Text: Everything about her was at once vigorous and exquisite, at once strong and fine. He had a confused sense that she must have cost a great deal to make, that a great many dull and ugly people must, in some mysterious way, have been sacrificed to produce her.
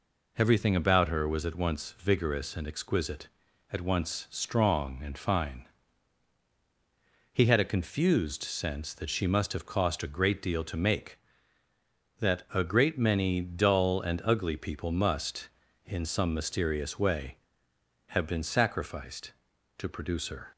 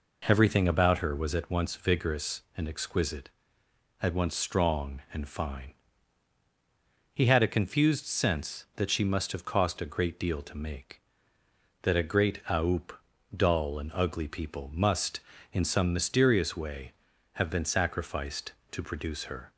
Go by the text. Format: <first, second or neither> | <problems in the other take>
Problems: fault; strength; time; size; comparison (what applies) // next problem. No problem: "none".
first | says "aoup" for "many"; at 12.4 s